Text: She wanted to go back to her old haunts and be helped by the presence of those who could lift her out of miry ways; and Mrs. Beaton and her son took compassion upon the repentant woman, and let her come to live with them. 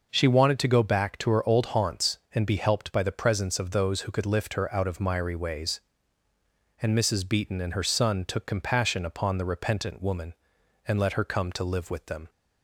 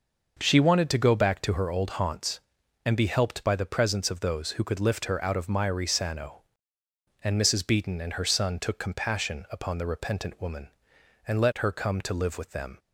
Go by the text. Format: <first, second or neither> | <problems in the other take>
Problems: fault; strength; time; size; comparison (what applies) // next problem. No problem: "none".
first | says "sano" for "ways"; at 5.8 s